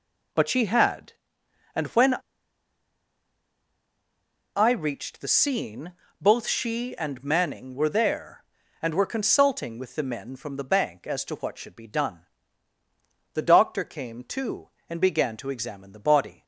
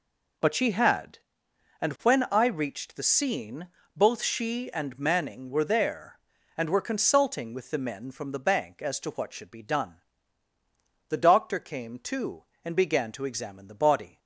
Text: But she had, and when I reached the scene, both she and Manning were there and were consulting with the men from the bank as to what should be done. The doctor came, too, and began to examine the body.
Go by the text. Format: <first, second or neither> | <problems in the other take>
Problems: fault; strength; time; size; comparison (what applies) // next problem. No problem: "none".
second | pauses between "when" and "I"; strong; at 2.1 s; 2.4 s long